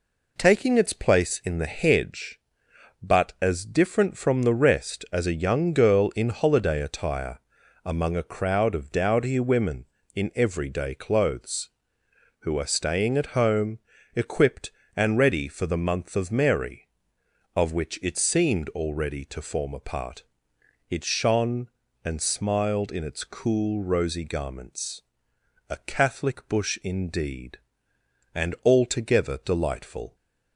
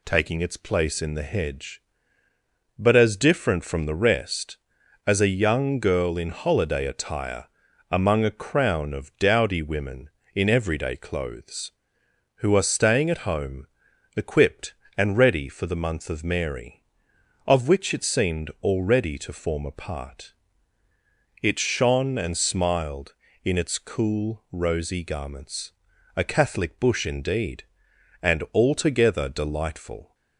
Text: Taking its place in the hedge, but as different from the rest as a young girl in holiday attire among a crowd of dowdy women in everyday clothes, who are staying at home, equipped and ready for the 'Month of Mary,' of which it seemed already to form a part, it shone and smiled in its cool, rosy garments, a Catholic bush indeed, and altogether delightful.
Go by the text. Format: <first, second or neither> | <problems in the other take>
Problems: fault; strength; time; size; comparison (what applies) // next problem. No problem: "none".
first | pauses between "attire" and "among"; noticeable; at 7.4 s; 0.46 s long; noticeable in the first // says "crown" for "crowd"; at 8.3 s